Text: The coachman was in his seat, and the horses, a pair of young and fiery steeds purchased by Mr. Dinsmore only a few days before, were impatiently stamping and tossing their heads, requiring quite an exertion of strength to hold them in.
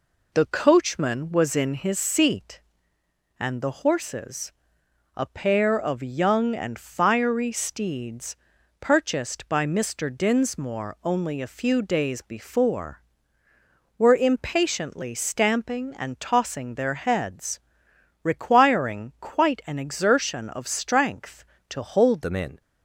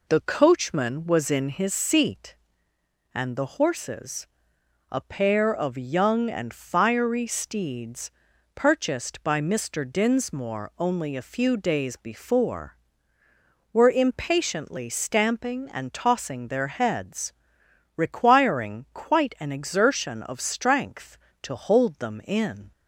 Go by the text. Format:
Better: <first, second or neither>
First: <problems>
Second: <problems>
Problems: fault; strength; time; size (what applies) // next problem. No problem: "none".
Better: second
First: pauses between "steeds" and "purchased"; at 8.3 s; 0.44 s long // changes voice at "them"; from 22.2 s on; 0.4 s long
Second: pauses between "steeds" and "purchased"; at 8.1 s; 0.44 s long